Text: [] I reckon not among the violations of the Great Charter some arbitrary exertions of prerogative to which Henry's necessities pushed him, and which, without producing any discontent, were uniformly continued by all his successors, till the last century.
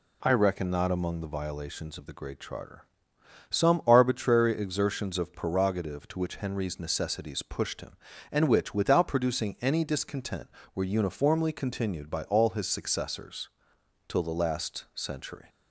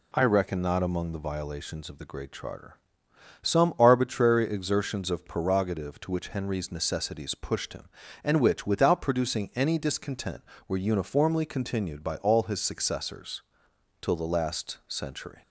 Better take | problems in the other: neither | pauses between "Charter" and "some"; noticeable; the same in both

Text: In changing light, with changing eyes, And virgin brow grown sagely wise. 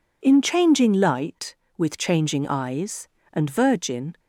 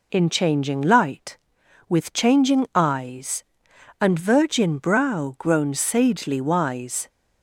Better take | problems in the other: second | stops before "brow grown sagely wise"; at 4.1 s

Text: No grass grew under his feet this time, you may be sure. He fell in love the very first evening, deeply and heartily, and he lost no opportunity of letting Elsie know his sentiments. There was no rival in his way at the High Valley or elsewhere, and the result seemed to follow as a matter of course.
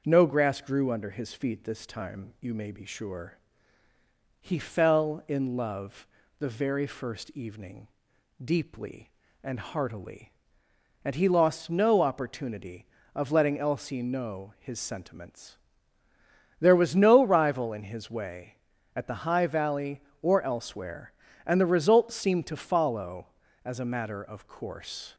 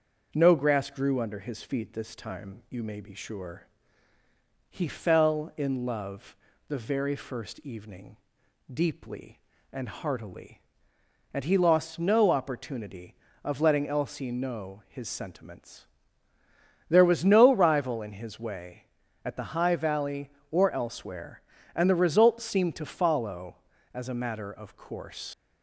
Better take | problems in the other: first | starts louder than the rest; until 1.3 s; 6.5 dB; also in the first // pauses between "love" and "the"; slight; at 6.3 s; 0.32 s long; slight in the first // leaves "course" unfinished; at 25.3 s; 105 ms

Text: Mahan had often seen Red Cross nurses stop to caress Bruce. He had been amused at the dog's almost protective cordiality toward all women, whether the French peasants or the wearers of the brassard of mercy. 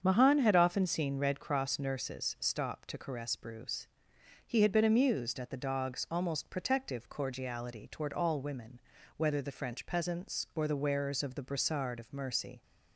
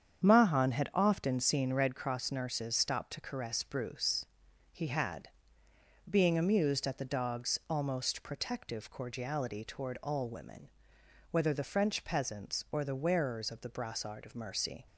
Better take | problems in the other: first | starts louder than the rest; strong; until 1.3 s; 8 dB; strong in the first // says "being" for "been"; at 6.0 s

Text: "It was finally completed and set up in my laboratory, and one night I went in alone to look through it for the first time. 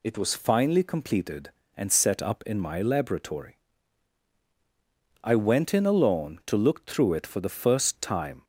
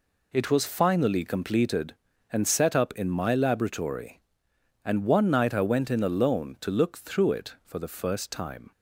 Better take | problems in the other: second | skips "and one night"; at 4.4 s

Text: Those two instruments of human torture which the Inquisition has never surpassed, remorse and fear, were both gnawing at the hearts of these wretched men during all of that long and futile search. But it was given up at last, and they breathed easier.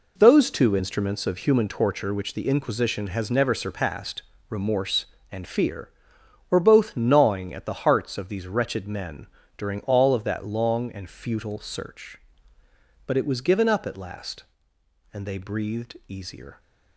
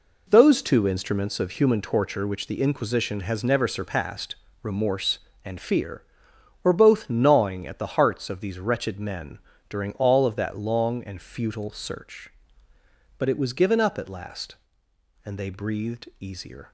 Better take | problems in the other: neither | pauses between "men" and "during"; slight; the same in both

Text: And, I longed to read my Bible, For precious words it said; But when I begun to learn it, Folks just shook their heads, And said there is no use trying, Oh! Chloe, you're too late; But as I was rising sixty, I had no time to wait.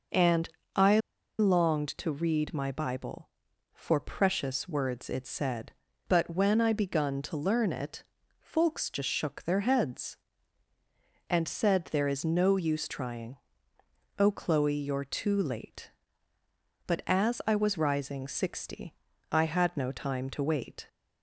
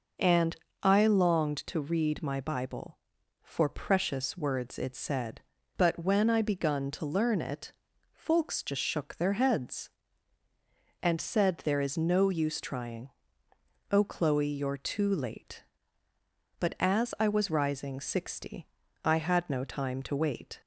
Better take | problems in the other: second | pauses between "I" and "longed"; at 0.9 s; 0.39 s long

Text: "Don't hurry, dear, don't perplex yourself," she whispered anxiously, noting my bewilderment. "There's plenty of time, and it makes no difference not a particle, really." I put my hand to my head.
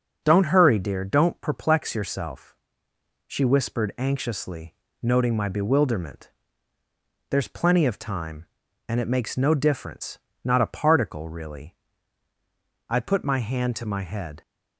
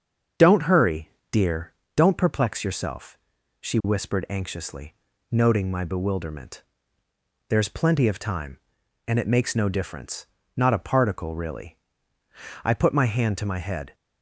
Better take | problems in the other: neither | starts louder than the rest; the same in both // pauses between "difference" and "not"; slight; the same in both

